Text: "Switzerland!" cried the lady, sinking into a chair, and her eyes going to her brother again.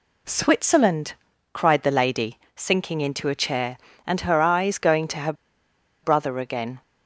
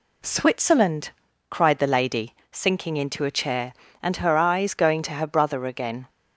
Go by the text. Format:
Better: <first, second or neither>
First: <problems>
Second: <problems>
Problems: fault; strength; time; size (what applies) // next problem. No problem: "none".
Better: second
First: pauses between "her" and "brother"; noticeable; at 5.3 s; 0.70 s long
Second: none